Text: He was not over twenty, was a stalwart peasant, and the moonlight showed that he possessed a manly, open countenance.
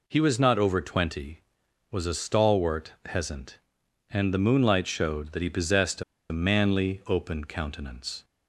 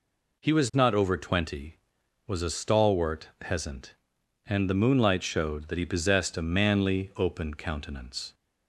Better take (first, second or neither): second